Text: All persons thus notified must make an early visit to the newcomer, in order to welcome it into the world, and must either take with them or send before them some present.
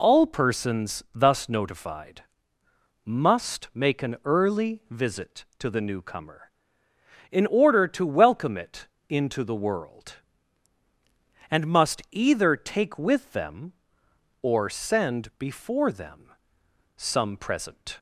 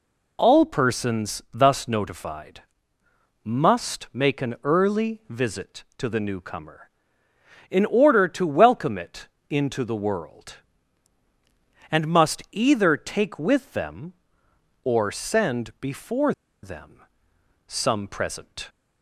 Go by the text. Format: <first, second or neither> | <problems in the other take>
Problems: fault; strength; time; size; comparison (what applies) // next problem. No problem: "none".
first | pauses between "notified" and "must"; noticeable; at 2.6 s; 0.82 s long; noticeable in the first // pauses between "it" and "into"; slight; at 9.2 s; 0.22 s long; slight in the first // pauses between "before" and "them"; slight; at 16.3 s; 0.30 s long // pauses between "them" and "some"; noticeable; at 17.0 s; 0.66 s long; noticeable in the first